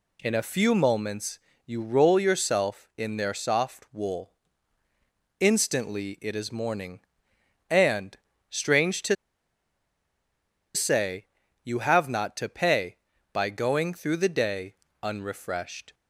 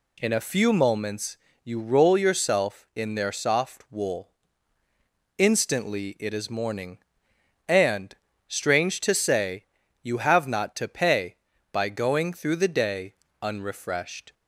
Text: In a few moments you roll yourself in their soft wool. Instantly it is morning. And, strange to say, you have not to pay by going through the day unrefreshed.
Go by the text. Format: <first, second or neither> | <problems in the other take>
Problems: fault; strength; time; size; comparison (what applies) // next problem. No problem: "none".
second | pauses between "moments" and "you"; slight; at 1.3 s; 0.26 s long; slight in the second // pauses between "to" and "say"; strong; at 9.1 s; 1.6 s long // pauses between "day" and "unrefreshed"; slight; at 14.7 s; 0.28 s long; slight in the second